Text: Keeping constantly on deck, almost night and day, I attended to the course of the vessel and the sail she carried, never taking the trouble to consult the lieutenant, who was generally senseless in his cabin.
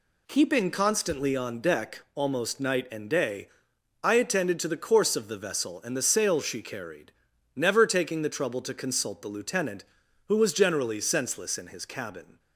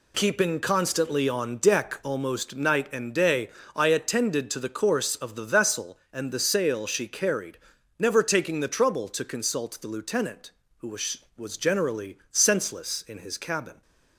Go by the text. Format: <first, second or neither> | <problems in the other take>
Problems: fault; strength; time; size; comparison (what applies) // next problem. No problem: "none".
first | says "was" twice; at 11.3 s